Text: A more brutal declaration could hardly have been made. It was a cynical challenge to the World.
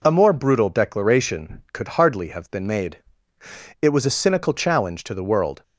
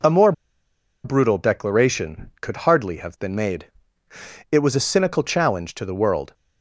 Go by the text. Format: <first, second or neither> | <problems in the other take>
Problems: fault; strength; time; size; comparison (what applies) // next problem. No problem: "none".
first | pauses between "more" and "brutal"; noticeable; at 0.3 s; 0.72 s long